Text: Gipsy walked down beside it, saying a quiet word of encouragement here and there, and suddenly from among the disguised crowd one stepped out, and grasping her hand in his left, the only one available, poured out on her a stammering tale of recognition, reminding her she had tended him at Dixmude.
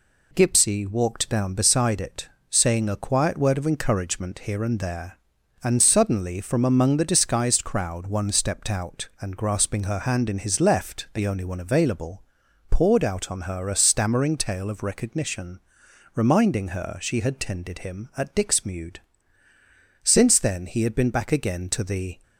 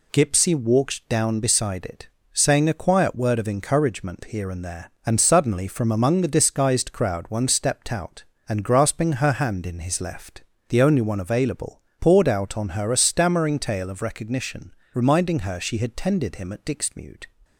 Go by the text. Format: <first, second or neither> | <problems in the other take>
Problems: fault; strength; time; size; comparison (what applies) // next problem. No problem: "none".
second | goes on to say "Since then he had been back again to the"; strong; from 20.0 s on; 2.1 s long